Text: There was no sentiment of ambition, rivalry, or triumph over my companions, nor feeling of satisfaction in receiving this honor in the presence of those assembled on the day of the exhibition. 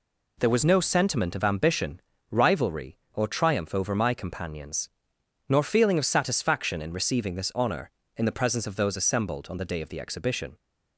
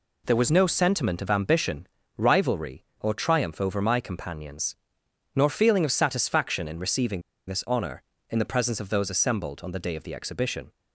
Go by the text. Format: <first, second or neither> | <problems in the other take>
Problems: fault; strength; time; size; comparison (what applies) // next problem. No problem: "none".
first | pauses between "receiving" and "this"; slight; at 7.2 s; 0.26 s long